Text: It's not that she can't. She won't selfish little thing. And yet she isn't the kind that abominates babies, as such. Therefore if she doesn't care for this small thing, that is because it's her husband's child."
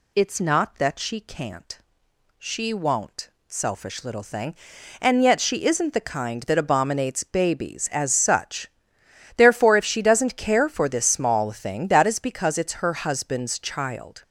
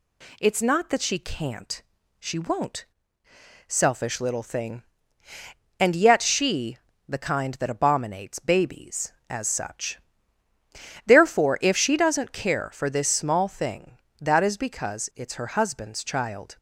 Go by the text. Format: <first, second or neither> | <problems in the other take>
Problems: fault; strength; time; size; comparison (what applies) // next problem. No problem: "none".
first | pauses between "won't" and "selfish"; noticeable; at 2.8 s; 0.82 s long; slight in the first // skips "isn't"; at 6.9 s